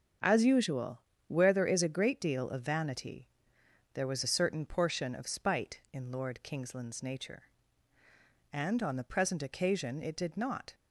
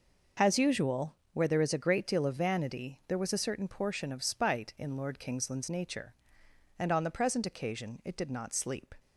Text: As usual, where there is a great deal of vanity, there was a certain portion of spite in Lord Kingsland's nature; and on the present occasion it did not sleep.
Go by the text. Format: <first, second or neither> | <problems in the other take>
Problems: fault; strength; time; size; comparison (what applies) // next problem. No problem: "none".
second | starts louder than the rest; until 1.5 s; 7 dB // stops before "sleep"; at 10.7 s